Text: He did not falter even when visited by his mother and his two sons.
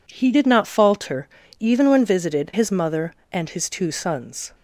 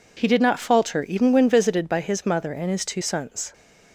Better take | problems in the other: second | pauses between "falter" and "even"; slight; at 1.2 s; 0.32 s long // skips "by"; at 2.5 s

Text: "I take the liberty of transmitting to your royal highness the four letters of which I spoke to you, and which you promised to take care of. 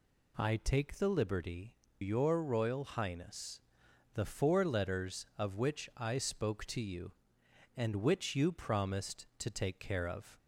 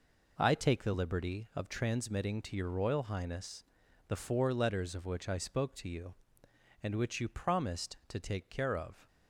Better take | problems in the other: second | skips "of transmitting to"; at 1.8 s // pauses between "highness" and "the"; noticeable; at 3.5 s; 0.54 s long; noticeable in the second

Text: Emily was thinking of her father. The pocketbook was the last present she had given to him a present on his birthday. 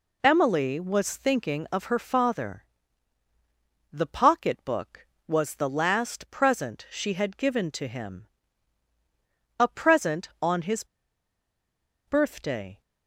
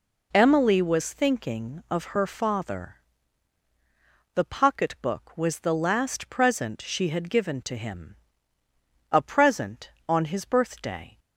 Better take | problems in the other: second | pauses between "him" and "a"; strong; at 8.2 s; 1.3 s long; noticeable in the second // pauses between "his" and "birthday"; at 10.8 s; 1.2 s long

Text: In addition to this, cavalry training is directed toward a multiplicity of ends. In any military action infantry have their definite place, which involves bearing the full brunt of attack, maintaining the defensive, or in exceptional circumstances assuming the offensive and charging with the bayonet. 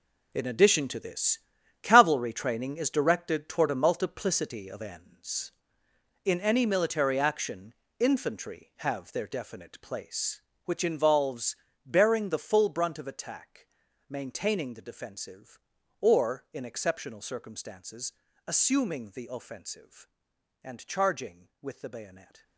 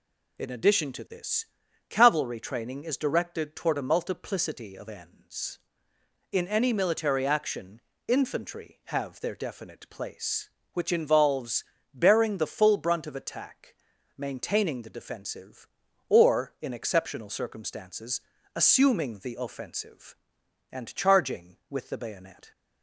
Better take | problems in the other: second | gets quieter; strong; throughout; 11.5 dB // pauses between "action" and "infantry"; slight; at 7.7 s; 0.24 s long; slight in the second // pauses between "involves" and "bearing"; slight; at 11.5 s; 0.30 s long; slight in the second // pauses between "circumstances" and "assuming"; slight; at 18.1 s; 0.34 s long; slight in the second

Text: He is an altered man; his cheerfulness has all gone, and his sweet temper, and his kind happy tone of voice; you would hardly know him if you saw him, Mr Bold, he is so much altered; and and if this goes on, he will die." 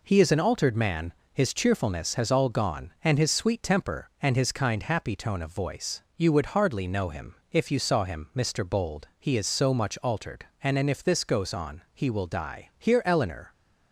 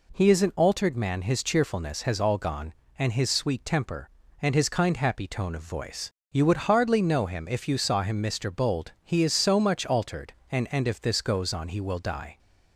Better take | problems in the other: second | pauses between "him" and "if"; slight; at 7.3 s; 0.18 s long // goes on to say "Here Eleanor"; noticeable; from 12.7 s on; 0.76 s long

